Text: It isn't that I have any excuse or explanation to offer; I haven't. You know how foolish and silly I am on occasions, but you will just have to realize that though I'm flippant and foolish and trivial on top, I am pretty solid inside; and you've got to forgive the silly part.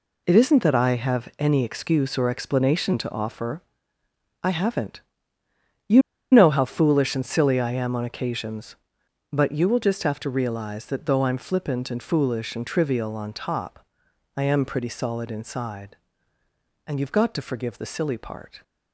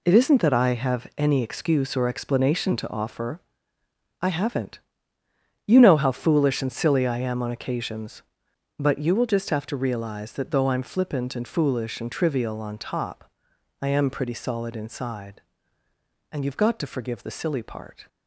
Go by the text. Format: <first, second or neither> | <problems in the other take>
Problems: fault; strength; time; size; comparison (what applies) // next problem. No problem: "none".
second | pauses between "You" and "know"; slight; at 6.0 s; 0.31 s long